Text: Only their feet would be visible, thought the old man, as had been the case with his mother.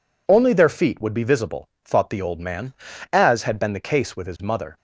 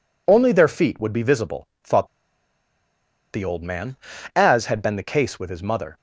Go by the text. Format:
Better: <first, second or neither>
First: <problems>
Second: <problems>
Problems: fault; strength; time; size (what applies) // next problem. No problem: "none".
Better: first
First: none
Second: pauses between "thought" and "the"; at 2.0 s; 1.2 s long